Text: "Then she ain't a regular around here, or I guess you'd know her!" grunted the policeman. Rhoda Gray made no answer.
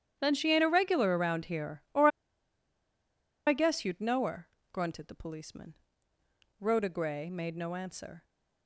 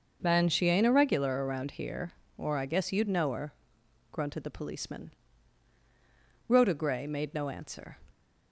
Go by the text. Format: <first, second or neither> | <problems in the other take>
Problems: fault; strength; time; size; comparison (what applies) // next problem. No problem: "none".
second | starts louder than the rest; strong; until 1.2 s; 10 dB // pauses between "or" and "I"; strong; at 2.0 s; 1.3 s long